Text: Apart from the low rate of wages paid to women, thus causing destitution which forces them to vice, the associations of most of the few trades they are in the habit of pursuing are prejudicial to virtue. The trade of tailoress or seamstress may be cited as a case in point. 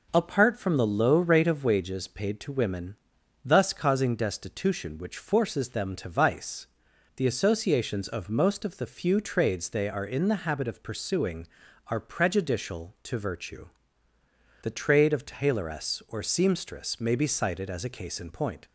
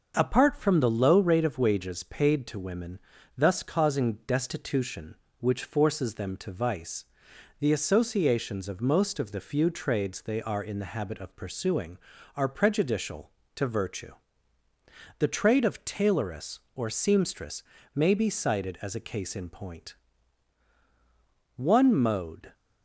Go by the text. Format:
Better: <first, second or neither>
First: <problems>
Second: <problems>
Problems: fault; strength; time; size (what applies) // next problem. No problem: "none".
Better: first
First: none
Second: starts louder than the rest; until 1.1 s; 6.5 dB // pauses between "seamstress" and "may"; slight; at 17.6 s; 0.32 s long // goes on to say "One mode"; noticeable; from 21.5 s on; 0.96 s long